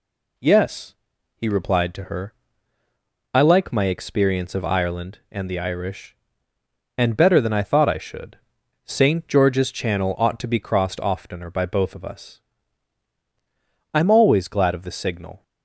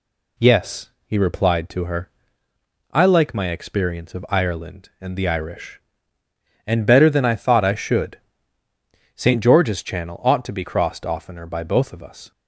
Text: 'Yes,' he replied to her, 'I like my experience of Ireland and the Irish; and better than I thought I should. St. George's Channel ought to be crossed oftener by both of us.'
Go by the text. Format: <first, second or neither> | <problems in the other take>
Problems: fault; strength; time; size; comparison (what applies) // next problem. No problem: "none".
second | goes on to say "I'm always glad of the signal"; from 13.9 s on; 1.4 s long